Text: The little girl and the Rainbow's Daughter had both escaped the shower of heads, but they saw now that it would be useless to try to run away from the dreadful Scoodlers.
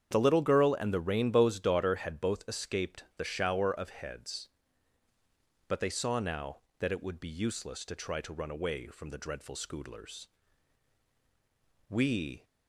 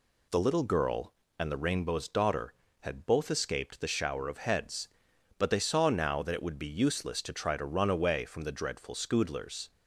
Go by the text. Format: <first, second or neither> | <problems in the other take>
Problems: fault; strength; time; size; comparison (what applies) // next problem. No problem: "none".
second | starts louder than the rest; strong; until 1.1 s; 8 dB // goes on to say "We"; from 11.8 s on; 0.56 s long